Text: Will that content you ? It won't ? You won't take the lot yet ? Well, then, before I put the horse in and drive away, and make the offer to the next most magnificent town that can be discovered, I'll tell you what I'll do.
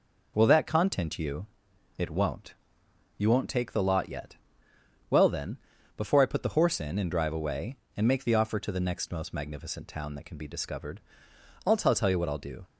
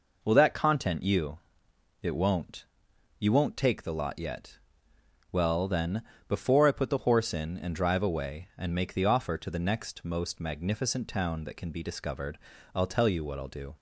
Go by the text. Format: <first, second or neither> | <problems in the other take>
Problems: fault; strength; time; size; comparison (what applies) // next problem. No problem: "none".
second | says "tell" twice; at 11.9 s